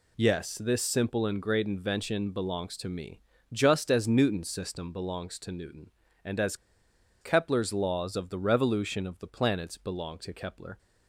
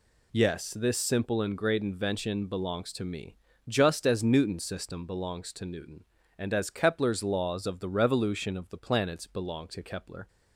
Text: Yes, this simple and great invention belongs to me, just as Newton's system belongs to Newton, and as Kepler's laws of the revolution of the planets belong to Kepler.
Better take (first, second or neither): second